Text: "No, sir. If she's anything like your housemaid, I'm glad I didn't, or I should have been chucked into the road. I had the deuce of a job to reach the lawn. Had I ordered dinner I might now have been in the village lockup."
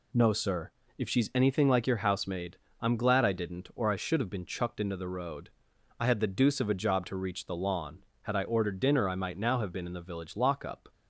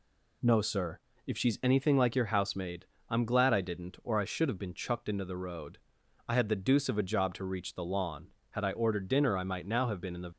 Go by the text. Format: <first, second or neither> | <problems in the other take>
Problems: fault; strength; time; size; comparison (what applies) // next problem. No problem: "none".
first | stops before "village lockup"; at 10.3 s